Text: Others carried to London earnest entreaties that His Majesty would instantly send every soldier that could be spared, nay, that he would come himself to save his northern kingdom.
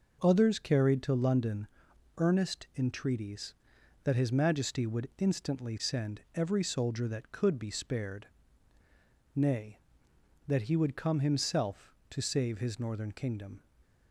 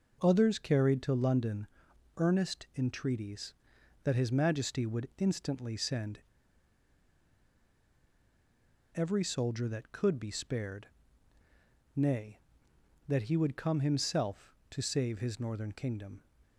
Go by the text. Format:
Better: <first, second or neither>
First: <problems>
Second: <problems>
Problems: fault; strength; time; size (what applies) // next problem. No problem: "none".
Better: first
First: pauses between "London" and "earnest"; noticeable; at 1.6 s; 0.48 s long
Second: pauses between "London" and "earnest"; noticeable; at 1.6 s; 0.48 s long // pauses between "send" and "every"; strong; at 6.1 s; 2.7 s long